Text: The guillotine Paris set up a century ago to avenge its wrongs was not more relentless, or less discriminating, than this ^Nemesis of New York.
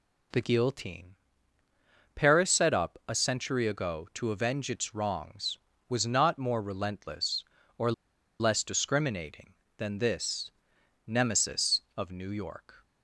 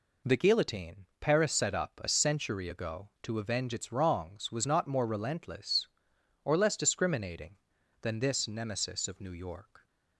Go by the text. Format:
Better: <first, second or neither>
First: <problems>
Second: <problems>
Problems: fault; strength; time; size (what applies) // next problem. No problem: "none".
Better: second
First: pauses between "guillotine" and "Paris"; at 1.1 s; 1.0 s long // pauses between "or" and "less"; noticeable; at 7.9 s; 0.48 s long // pauses between "this" and "Nemesis"; noticeable; at 10.5 s; 0.56 s long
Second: none